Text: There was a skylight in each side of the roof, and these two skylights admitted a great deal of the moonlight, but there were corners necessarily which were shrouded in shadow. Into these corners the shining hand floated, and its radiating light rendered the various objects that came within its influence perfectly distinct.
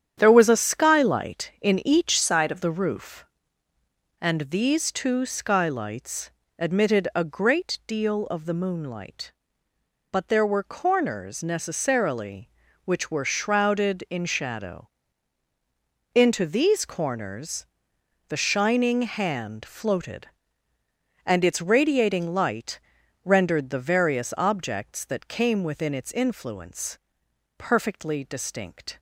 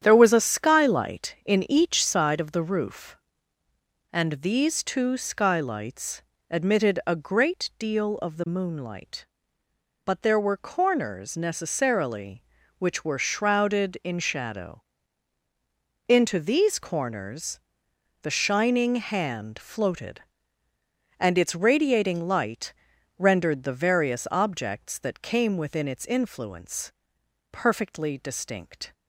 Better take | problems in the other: second | starts louder than the rest; strong; until 1.1 s; 9 dB; strong in the second // changes voice from "side" to "of"; from 2.2 to 2.6 s; 0.4 s long // pauses between "skylights" and "admitted"; slight; at 6.3 s; 0.28 s long; slight in the second // pauses between "corners" and "the"; noticeable; at 17.6 s; 0.62 s long; noticeable in the second // pauses between "light" and "rendered"; at 22.8 s; 0.42 s long; also in the second // pauses between "influence" and "perfectly"; noticeable; at 26.9 s; 0.60 s long; noticeable in the second

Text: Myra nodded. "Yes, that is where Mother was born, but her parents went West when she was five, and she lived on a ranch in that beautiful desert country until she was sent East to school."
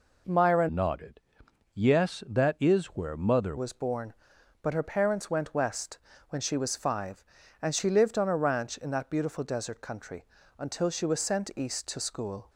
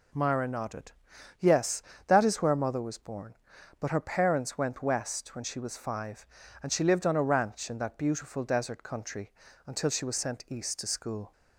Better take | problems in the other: second | changes voice from "nodded" to "Mother"; from 0.6 to 3.5 s; 2.9 s long // pauses between "West" and "when"; slight; at 5.9 s; 0.32 s long // pauses between "country" and "until"; slight; at 10.2 s; 0.34 s long; also in the second

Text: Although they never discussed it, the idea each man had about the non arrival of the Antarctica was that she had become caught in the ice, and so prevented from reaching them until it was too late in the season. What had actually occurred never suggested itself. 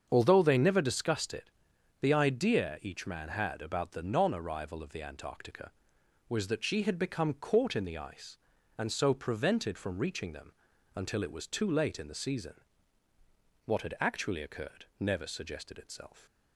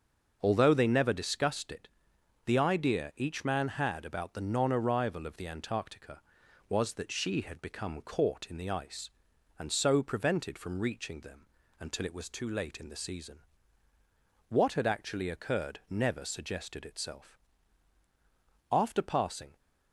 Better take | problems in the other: first | starts louder than the rest; until 1.4 s; 6 dB; also in the first // pauses between "them" and "until"; slight; at 11.4 s; 0.34 s long; also in the first // goes on to say "After passing"; noticeable; from 18.7 s on; 0.86 s long

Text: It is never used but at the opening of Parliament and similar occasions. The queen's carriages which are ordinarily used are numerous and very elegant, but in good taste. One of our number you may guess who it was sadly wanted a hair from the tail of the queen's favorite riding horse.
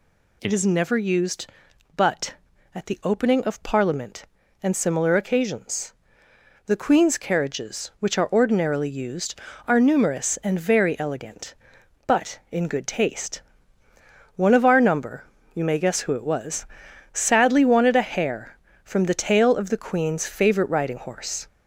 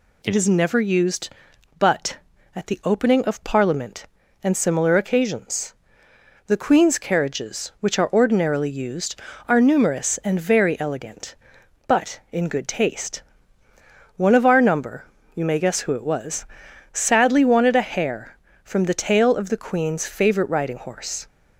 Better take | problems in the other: second | gets louder; slight; throughout; 3 dB // pauses between "number" and "you"; slight; at 15.2 s; 0.30 s long; slight in the second // pauses between "was" and "sadly"; noticeable; at 16.6 s; 0.48 s long; noticeable in the second

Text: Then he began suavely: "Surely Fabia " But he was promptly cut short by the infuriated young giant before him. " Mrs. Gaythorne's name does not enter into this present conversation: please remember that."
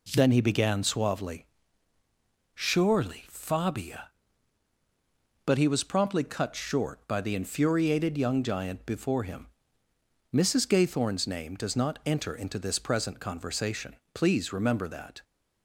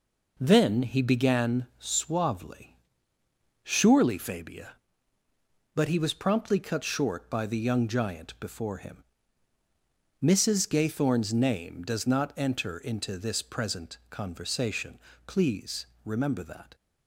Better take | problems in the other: first | skips "infuriated"; at 7.5 s // pauses between "please" and "remember"; slight; at 15.8 s; 0.16 s long

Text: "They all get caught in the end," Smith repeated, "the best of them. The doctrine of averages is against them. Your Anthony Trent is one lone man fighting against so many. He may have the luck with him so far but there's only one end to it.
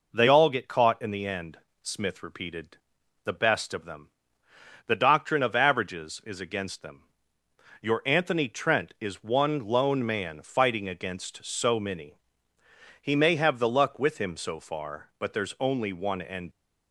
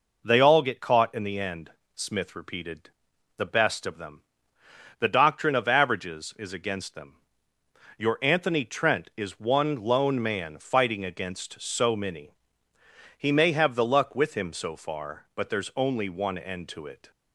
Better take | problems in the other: second | stops before "to it"; at 16.5 s

